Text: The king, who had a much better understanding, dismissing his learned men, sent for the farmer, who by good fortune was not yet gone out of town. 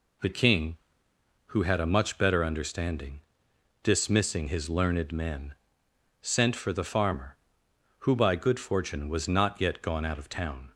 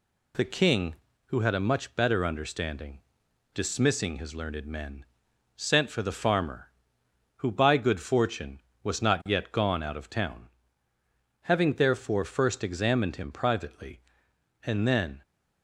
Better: first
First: none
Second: goes on to say "Having therefore first examined him privately and then"; strong; from 11.4 s on; 3.8 s long

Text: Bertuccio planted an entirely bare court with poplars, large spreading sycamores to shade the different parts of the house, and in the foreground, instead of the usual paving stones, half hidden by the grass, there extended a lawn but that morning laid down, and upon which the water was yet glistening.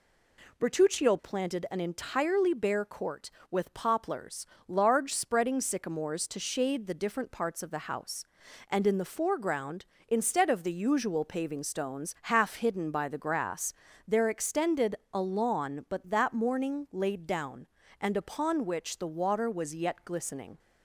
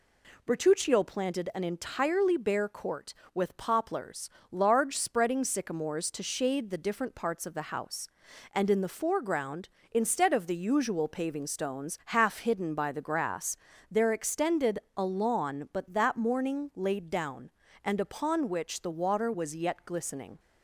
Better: neither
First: pauses between "extended" and "a"; slight; at 14.9 s; 0.18 s long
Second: pauses between "extended" and "a"; slight; at 14.7 s; 0.18 s long

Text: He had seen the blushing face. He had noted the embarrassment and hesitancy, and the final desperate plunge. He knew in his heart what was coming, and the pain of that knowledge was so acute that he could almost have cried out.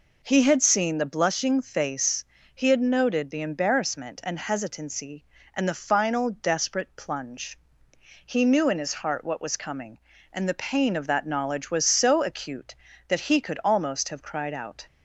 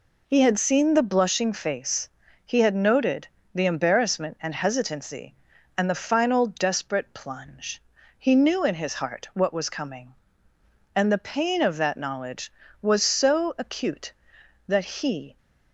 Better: first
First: none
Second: pauses between "noted" and "the"; slight; at 3.2 s; 0.26 s long // stops before "could almost have cried out"; at 15.3 s

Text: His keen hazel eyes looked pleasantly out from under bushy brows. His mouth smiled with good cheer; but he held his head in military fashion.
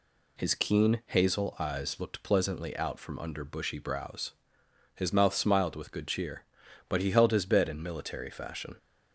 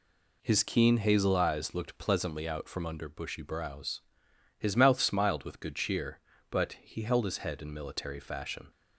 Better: second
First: says "bed" for "head"; at 7.4 s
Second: none

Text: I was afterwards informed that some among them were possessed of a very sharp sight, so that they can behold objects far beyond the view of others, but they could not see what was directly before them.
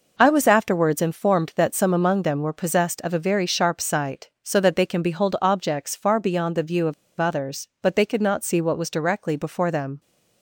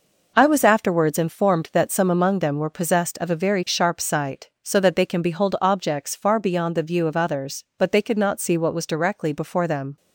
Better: second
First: pauses between "of" and "others"; slight; at 6.9 s; 0.25 s long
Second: none

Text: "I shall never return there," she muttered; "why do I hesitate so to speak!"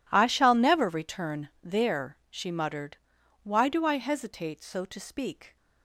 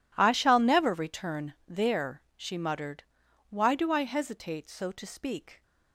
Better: neither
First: none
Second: none

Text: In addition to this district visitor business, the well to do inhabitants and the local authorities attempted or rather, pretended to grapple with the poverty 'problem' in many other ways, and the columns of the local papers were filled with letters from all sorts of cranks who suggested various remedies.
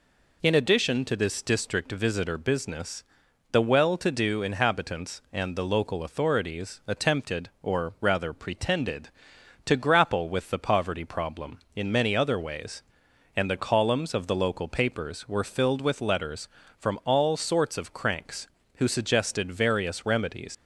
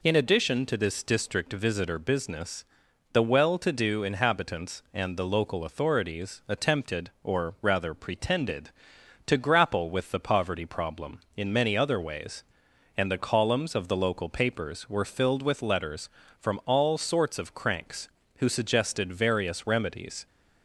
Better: second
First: leaves "remedies" unfinished; at 20.5 s; 100 ms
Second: none

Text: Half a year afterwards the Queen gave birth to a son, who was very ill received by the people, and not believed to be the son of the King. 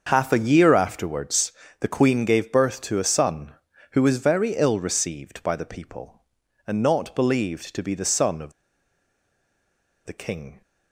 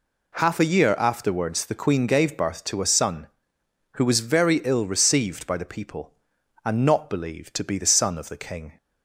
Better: second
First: starts louder than the rest; until 1.0 s; 6.5 dB // pauses between "afterwards" and "the"; slight; at 1.5 s; 0.30 s long // pauses between "of" and "the"; strong; at 8.5 s; 1.5 s long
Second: none

